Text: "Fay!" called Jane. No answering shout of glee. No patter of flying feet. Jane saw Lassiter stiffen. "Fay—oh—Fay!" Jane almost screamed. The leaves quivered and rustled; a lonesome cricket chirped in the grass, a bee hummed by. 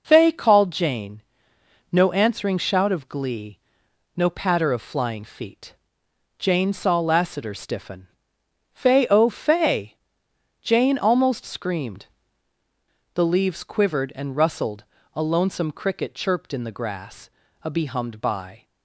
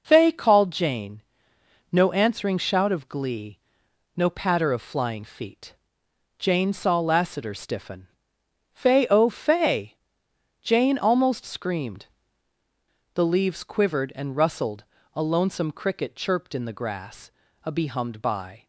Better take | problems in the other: neither | none

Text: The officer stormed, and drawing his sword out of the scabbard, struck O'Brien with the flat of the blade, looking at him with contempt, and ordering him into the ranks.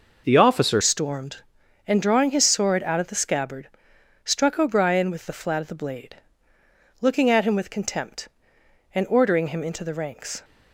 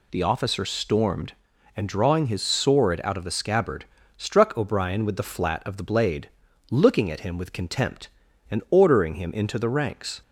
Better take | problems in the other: second | changes voice at "stormed"; from 0.8 s on; 9.6 s long

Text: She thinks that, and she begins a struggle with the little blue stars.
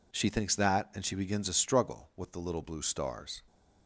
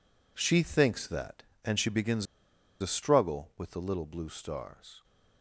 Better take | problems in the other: first | pauses between "begins" and "a"; noticeable; at 2.2 s; 0.55 s long

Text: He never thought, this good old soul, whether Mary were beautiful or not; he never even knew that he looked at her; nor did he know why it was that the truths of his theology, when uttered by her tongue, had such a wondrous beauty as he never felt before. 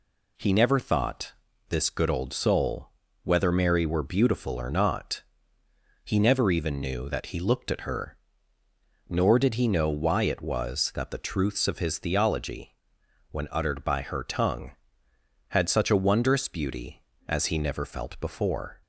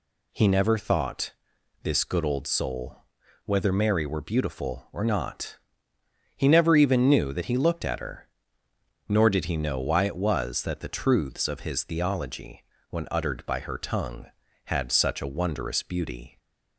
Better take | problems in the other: first | stops before "as he never felt before"; at 16.3 s

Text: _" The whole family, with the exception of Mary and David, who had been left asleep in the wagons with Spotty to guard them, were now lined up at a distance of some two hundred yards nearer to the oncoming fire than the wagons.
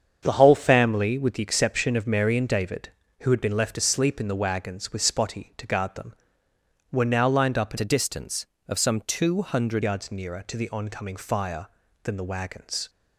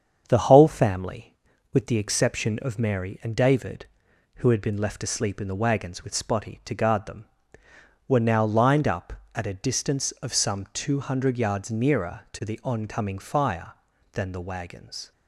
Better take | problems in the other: second | starts louder than the rest; strong; until 1.2 s; 7.5 dB; strong in the second // changes voice from "a" to "hundred"; from 7.7 to 9.8 s; 2.1 s long

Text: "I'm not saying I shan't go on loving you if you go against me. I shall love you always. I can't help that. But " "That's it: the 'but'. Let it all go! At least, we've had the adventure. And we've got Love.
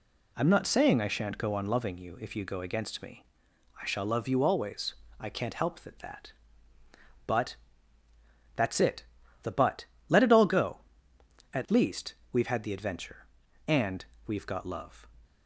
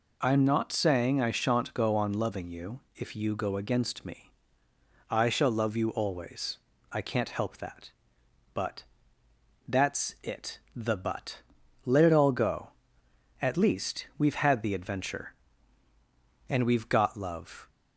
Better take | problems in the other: second | says "that" twice; at 5.9 s // pauses between "And" and "we've"; slight; at 14.0 s; 0.22 s long

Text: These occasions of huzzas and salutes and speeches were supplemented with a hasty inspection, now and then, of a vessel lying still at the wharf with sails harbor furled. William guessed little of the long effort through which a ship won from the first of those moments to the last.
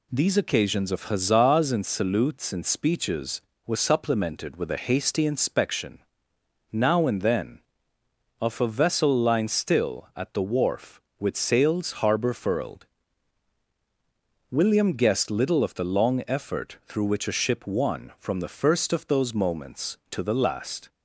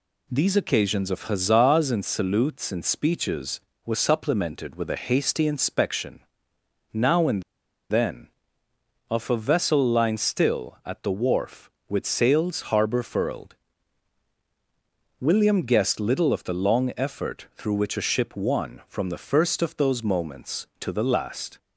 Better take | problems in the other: first | pauses between "and" and "then"; noticeable; at 7.4 s; 0.49 s long

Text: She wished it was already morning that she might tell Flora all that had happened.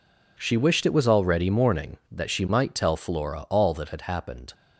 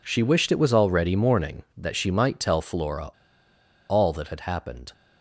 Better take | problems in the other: first | pauses between "Flora" and "all"; noticeable; at 3.0 s; 0.79 s long

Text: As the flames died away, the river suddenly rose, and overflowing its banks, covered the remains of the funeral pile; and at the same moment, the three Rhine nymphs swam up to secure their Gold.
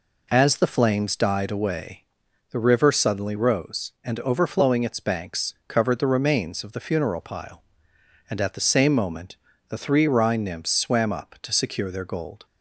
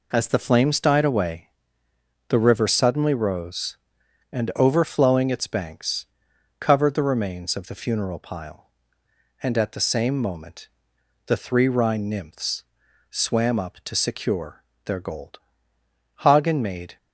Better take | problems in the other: first | pauses between "nymphs" and "swam"; at 12.6 s; 0.44 s long // pauses between "secure" and "their"; slight; at 14.6 s; 0.20 s long // goes on to say "Hagen made"; noticeable; from 16.1 s on; 0.80 s long

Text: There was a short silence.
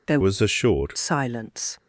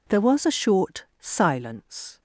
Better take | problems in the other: second | changes voice from "was" to "short"; from 0.2 to 0.9 s; 0.7 s long

